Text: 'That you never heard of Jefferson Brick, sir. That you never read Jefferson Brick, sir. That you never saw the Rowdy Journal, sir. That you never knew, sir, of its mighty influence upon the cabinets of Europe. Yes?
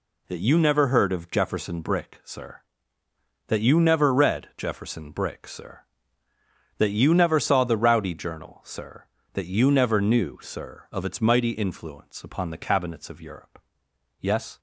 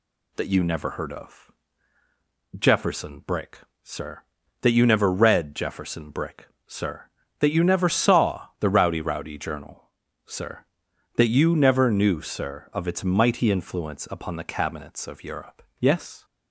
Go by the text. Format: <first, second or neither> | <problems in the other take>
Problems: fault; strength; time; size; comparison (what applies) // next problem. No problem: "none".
first | pauses between "of" and "Jefferson"; at 1.5 s; 1.0 s long // says "Rowdy" twice; at 9.0 s